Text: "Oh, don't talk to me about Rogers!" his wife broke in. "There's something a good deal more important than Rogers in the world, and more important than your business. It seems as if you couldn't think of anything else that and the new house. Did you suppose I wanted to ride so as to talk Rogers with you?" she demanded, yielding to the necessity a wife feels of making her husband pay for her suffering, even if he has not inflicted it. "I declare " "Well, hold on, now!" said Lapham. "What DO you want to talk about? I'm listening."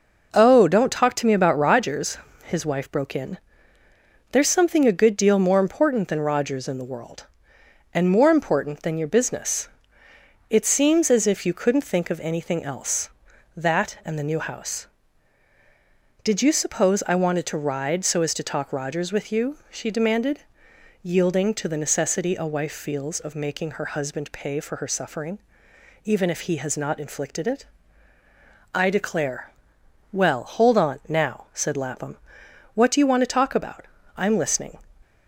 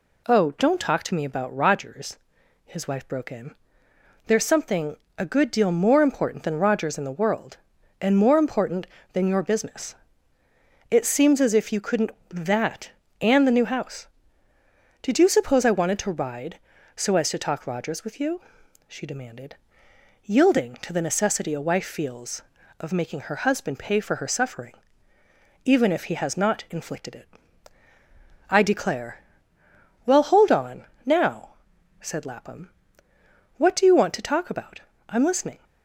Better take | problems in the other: first | pauses between "something" and "a"; slight; at 4.9 s; 0.22 s long // skips "think of anything else"; at 12.1 s

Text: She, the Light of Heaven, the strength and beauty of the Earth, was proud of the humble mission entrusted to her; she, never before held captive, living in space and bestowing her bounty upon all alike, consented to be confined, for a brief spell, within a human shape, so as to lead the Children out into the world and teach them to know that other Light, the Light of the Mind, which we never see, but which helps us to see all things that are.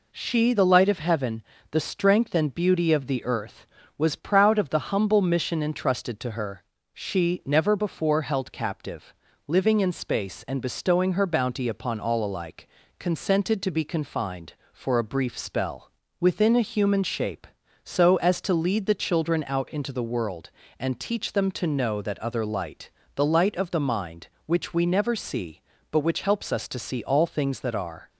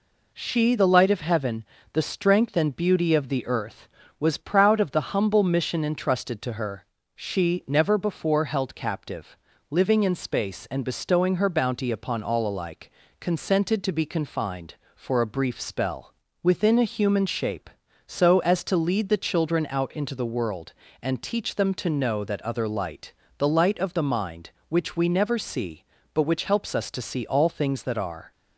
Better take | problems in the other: neither | none

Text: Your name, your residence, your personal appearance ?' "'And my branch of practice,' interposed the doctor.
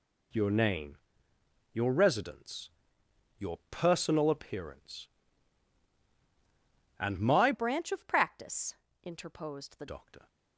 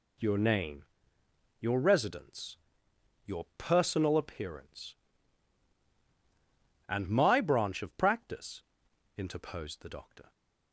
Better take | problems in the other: second | changes voice from "branch" to "the"; from 7.5 to 9.8 s; 2.3 s long

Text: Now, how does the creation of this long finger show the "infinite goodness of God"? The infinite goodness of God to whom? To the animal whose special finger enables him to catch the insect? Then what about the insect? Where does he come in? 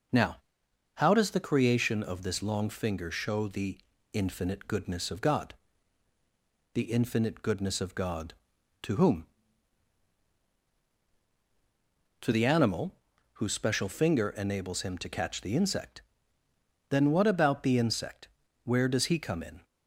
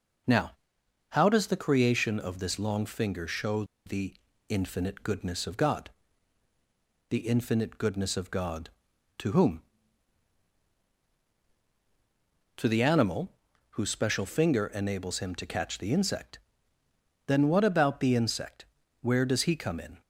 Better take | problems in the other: first | pauses between "show" and "the"; slight; at 3.6 s; 0.21 s long // pauses between "the" and "infinite"; slight; at 4.1 s; 0.36 s long; slight in the first // pauses between "animal" and "whose"; at 13.3 s; 0.40 s long; also in the first

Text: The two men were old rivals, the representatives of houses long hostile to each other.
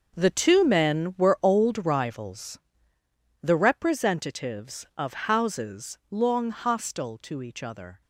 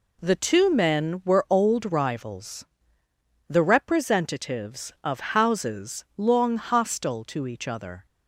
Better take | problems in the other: second | gets quieter; strong; throughout; 11.5 dB

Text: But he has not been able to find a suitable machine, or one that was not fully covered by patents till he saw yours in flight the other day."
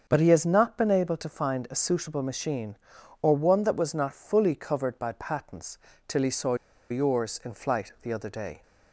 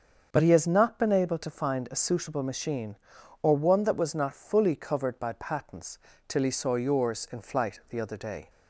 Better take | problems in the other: second | starts louder than the rest; until 1.0 s; 7 dB; also in the second // pauses between "patents" and "till"; slight; at 5.7 s; 0.30 s long; slight in the second // pauses between "saw" and "yours"; slight; at 6.5 s; 0.35 s long

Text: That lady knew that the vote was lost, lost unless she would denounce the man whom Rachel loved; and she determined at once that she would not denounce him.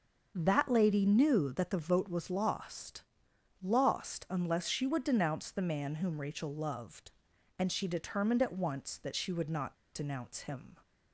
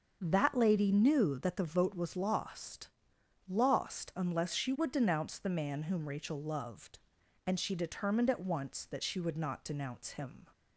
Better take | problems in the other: second | starts louder than the rest; until 1.3 s; 6.5 dB; also in the second // pauses between "not" and "denounce"; slight; at 9.7 s; 0.19 s long

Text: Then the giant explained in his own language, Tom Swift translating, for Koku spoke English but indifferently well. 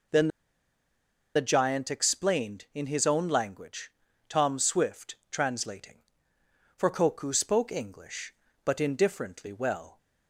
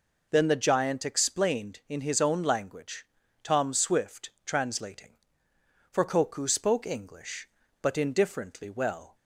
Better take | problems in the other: second | pauses between "Then" and "the"; at 0.2 s; 1.0 s long

